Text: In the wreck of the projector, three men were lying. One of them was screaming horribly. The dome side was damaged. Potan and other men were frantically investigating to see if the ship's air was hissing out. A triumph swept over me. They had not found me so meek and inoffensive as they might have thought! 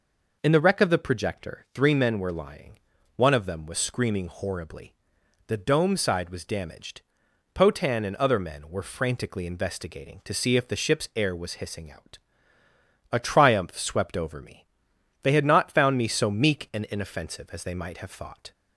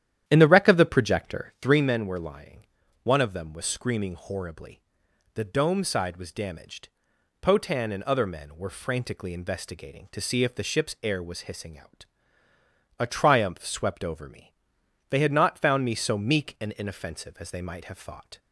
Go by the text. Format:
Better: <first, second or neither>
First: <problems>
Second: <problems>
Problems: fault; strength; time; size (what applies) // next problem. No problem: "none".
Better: first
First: none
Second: starts louder than the rest; strong; until 1.9 s; 11 dB